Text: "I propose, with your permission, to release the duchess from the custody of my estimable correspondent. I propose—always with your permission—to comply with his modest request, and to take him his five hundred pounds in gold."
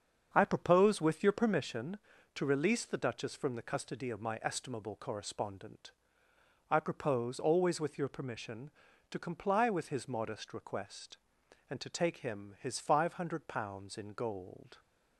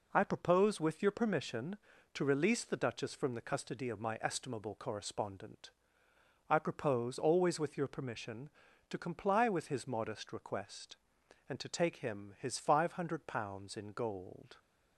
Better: second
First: starts louder than the rest; until 1.7 s; 7 dB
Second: none

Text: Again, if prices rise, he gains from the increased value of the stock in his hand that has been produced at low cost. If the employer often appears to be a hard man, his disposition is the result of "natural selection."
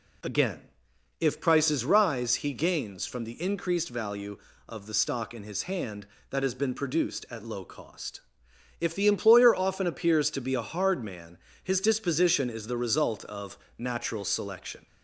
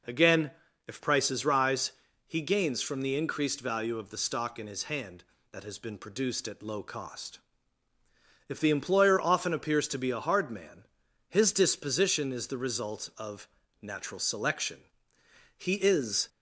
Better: first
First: pauses between "of" and "natural"; slight; at 13.5 s; 0.20 s long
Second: pauses between "of" and "natural"; slight; at 13.4 s; 0.34 s long // goes on to say "He is"; noticeable; from 15.5 s on; 0.72 s long

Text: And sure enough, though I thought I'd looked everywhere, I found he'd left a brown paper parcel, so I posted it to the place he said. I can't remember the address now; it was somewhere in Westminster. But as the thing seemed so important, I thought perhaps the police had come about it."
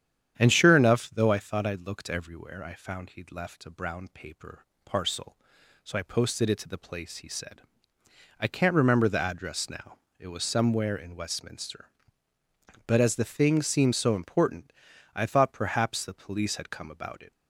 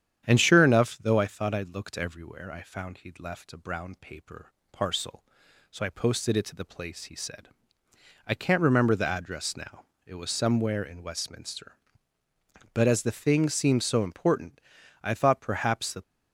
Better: first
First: starts louder than the rest; strong; until 1.4 s; 9 dB // pauses between "paper" and "parcel"; slight; at 4.6 s; 0.20 s long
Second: starts louder than the rest; strong; until 1.2 s; 9 dB // pauses between "paper" and "parcel"; slight; at 4.5 s; 0.20 s long // stops before "police had come about it"; at 16.0 s

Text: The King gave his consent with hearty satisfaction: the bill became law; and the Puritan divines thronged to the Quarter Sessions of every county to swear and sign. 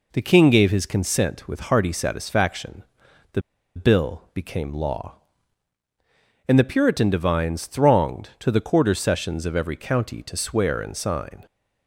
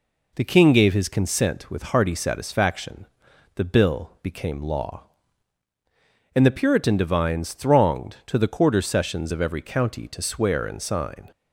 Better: second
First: pauses between "the" and "bill"; slight; at 3.4 s; 0.35 s long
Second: none

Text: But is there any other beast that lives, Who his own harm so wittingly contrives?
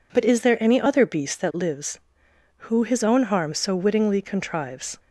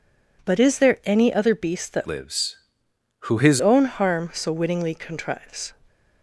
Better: first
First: none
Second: changes voice from "lives" to "his"; from 2.0 to 3.6 s; 1.6 s long

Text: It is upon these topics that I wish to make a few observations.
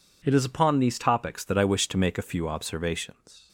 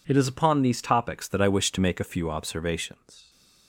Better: neither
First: none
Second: none

